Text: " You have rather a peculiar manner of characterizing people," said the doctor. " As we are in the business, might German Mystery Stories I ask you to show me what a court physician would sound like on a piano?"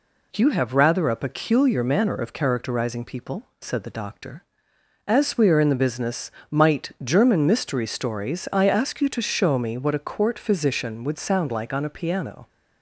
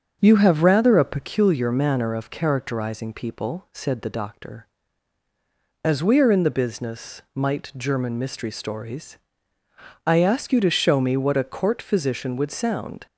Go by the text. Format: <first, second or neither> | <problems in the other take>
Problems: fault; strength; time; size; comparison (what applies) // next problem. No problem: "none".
first | starts louder than the rest; strong; until 1.2 s; 8.5 dB // pauses between "Stories" and "I"; noticeable; at 9.1 s; 0.90 s long // stops before "like on a piano"; at 13.0 s